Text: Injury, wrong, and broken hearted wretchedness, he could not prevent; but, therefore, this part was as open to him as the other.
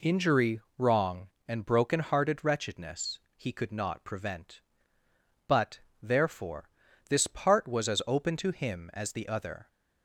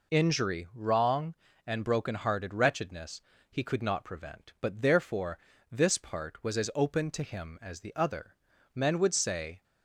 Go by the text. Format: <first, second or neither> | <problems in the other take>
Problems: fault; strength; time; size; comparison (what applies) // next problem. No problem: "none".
first | goes on to say "Men would say"; noticeable; from 8.7 s on; 0.90 s long